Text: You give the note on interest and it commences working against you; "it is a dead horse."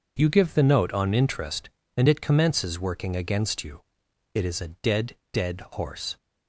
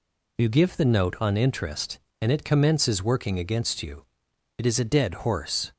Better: second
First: says "dead" twice; at 5.3 s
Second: none

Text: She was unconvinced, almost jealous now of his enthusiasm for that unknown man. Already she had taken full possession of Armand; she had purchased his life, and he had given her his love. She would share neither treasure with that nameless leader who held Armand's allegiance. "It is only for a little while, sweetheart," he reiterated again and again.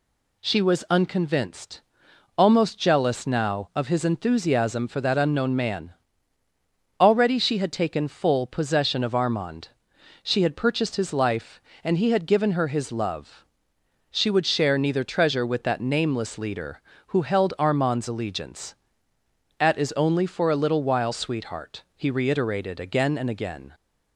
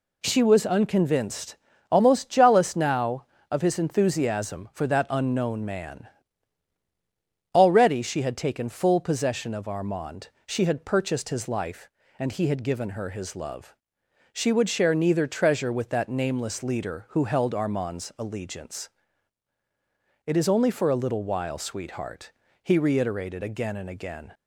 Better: second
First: says "At" for "It"; at 19.5 s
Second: none

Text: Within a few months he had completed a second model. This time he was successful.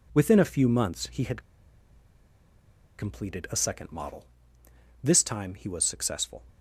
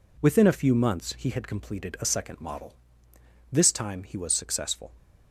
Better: second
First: pauses between "had" and "completed"; strong; at 1.4 s; 1.5 s long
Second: none

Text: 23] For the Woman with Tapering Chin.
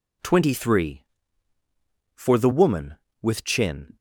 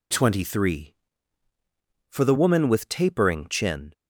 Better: second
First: skips "Tapering"; at 3.4 s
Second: none

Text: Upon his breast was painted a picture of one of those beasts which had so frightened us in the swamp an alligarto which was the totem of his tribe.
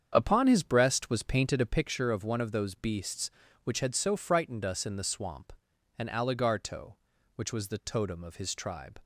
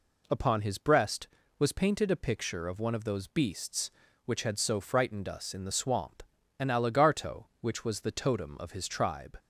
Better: second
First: starts louder than the rest; strong; until 1.8 s; 7.5 dB // pauses between "swamp" and "an"; noticeable; at 5.5 s; 0.46 s long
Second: pauses between "swamp" and "an"; slight; at 6.2 s; 0.36 s long

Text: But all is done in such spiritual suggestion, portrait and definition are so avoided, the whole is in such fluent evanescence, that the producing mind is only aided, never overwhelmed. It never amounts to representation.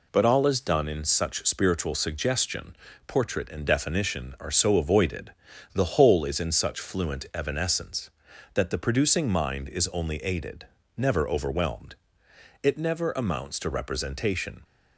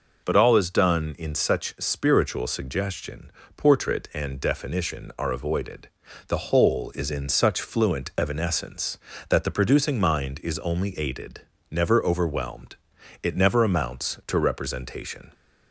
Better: first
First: none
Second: skips "so"; at 5.3 s

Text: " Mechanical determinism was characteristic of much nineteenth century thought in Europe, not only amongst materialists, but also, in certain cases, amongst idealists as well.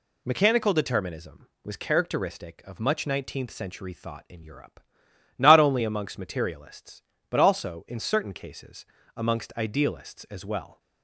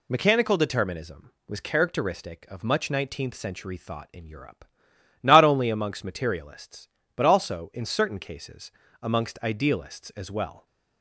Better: neither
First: none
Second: none

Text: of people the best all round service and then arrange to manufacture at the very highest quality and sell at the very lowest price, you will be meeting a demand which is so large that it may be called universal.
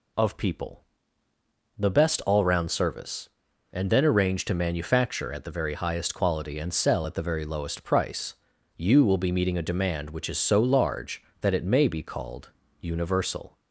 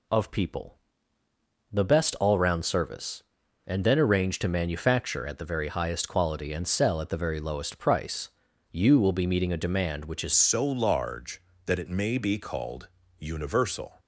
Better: first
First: pauses between "people" and "the"; noticeable; at 0.8 s; 0.96 s long // pauses between "called" and "universal"; slight; at 12.4 s; 0.30 s long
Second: pauses between "people" and "the"; noticeable; at 0.7 s; 0.96 s long // changes voice at "so"; from 10.3 s on; 3.6 s long // pauses between "called" and "universal"; slight; at 12.8 s; 0.28 s long

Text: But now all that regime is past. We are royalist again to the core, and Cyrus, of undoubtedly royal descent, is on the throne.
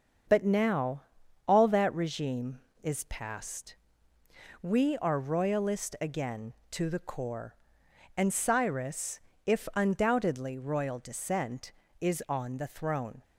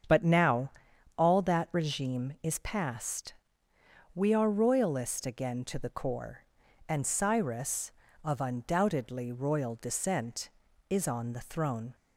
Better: second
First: starts louder than the rest; until 1.7 s; 6.5 dB // pauses between "now" and "all"; at 1.0 s; 0.44 s long // says "if" for "of"; at 9.4 s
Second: starts louder than the rest; strong; until 1.5 s; 7.5 dB // pauses between "now" and "all"; noticeable; at 0.7 s; 0.46 s long

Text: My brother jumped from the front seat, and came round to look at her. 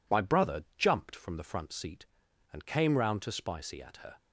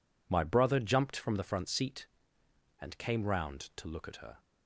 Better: second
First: says "spicy" for "look"; at 3.3 s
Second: none

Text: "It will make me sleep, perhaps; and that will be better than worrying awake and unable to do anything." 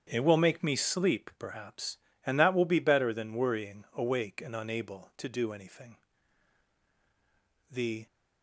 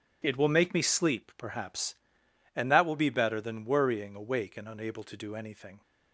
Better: second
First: starts louder than the rest; strong; until 1.1 s; 8.5 dB // goes on to say "The"; slight; from 7.6 s on; 0.36 s long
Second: none

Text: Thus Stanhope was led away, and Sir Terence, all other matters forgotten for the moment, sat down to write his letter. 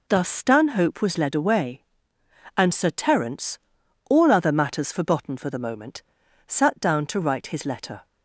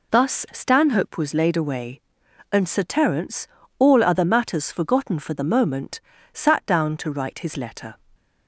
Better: first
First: none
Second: says "laid" for "led"; at 1.3 s

